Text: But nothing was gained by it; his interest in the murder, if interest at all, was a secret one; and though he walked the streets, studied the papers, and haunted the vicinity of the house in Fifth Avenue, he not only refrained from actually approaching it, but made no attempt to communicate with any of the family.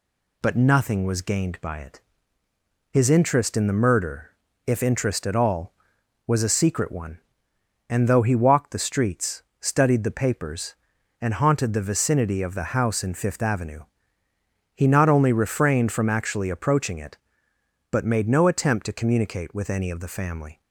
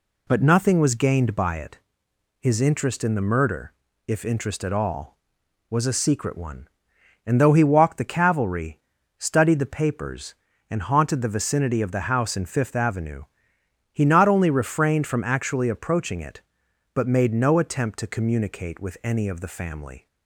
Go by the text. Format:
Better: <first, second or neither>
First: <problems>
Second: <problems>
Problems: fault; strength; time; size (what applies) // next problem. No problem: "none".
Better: first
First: none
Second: says "cavalry" for "streets"; at 8.1 s